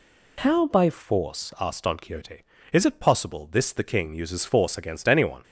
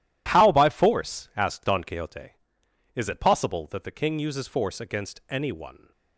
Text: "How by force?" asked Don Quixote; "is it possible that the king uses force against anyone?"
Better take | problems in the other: second | says "this" for "that"; at 3.5 s

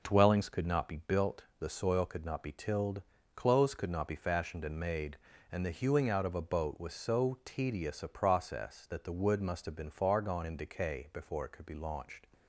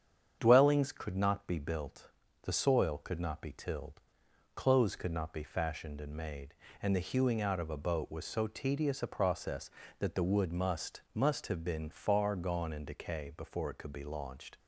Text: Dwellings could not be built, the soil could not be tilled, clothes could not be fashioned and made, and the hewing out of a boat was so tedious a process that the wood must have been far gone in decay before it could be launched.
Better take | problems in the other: first | starts louder than the rest; strong; until 1.4 s; 8 dB // says "must" twice; at 11.1 s

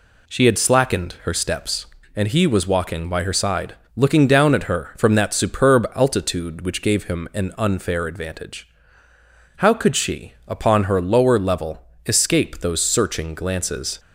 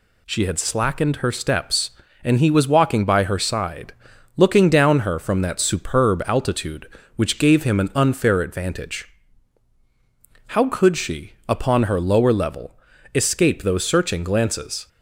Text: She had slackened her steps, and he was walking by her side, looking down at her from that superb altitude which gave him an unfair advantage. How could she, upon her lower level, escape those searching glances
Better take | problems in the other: first | skips "at"; at 4.9 s

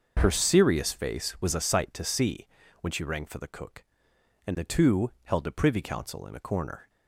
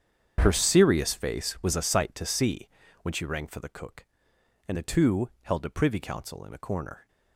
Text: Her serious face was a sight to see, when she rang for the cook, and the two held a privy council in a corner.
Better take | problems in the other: first | gets quieter; strong; throughout; 15 dB // starts louder than the rest; strong; until 1.4 s; 8 dB; noticeable in the first

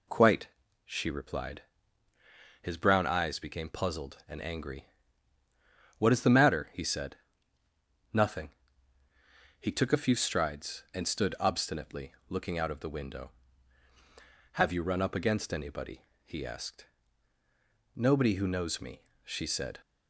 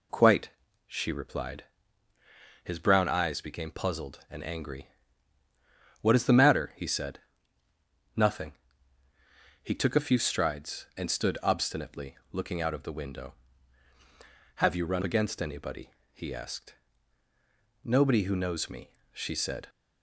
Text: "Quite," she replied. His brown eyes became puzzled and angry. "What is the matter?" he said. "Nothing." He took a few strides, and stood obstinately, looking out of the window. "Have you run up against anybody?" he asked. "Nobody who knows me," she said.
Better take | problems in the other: first | skips "up"; at 15.0 s

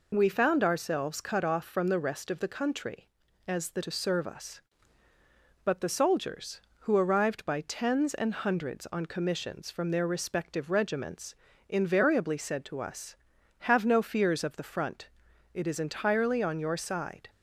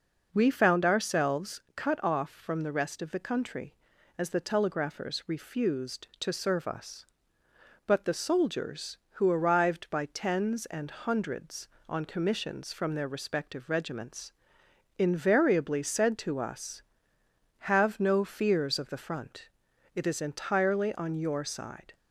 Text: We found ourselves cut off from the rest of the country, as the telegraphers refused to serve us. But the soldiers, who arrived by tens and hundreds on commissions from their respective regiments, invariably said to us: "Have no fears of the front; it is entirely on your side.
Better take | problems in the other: second | skips "telegraphers refused"; at 3.8 s

